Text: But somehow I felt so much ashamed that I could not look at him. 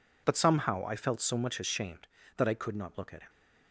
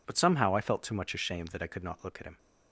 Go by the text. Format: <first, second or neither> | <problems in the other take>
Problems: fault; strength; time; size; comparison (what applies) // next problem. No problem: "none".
first | says "too" for "so"; at 0.8 s